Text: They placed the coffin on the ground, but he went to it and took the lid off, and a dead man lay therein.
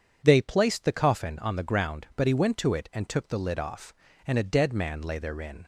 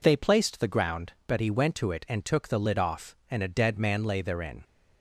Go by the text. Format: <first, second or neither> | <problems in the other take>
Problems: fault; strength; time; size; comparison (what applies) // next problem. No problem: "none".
first | skips "coffin on the"; at 0.6 s